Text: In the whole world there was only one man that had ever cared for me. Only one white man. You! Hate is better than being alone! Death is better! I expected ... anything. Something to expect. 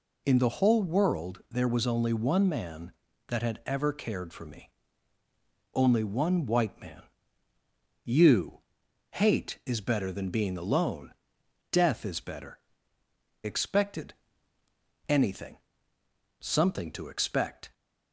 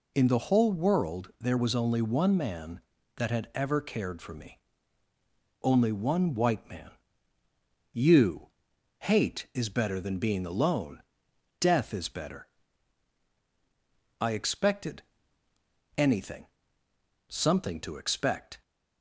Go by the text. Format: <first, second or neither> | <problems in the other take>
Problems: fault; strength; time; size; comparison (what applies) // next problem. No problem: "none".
second | skips "I"; at 13.0 s